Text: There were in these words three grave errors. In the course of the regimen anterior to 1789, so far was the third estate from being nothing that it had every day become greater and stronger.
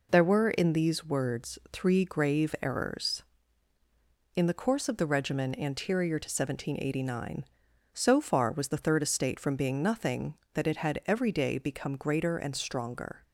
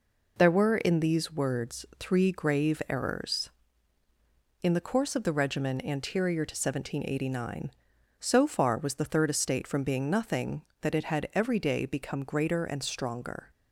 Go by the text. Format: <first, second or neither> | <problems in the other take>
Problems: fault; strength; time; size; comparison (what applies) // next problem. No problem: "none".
neither | none